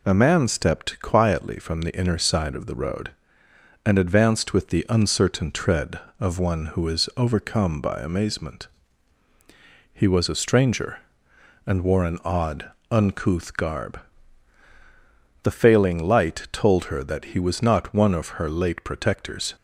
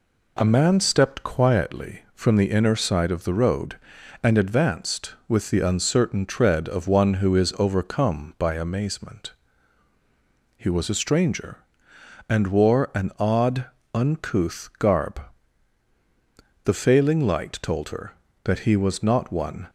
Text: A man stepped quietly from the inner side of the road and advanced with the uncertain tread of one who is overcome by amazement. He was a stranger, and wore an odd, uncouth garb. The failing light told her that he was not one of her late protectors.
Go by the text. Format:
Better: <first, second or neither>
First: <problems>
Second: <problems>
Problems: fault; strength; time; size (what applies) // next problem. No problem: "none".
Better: first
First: none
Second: stops before "of her late protectors"; at 19.6 s